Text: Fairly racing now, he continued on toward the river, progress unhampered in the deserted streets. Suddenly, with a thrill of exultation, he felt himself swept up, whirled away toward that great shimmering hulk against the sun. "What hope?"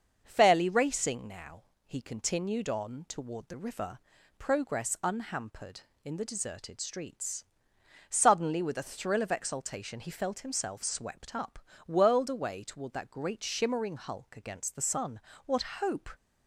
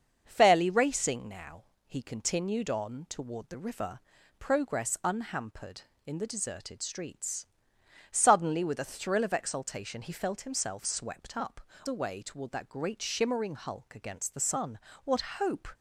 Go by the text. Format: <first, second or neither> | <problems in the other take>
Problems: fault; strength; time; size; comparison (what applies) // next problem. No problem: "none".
first | starts louder than the rest; until 1.2 s; 6.5 dB; also in the first // skips "whirled"; at 11.7 s // pauses between "What" and "hope"; slight; at 15.2 s; 0.18 s long; slight in the first